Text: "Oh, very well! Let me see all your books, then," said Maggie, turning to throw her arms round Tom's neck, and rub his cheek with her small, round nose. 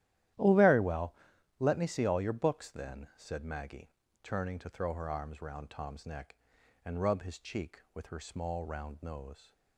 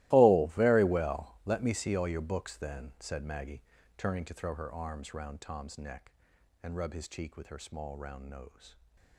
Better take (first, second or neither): first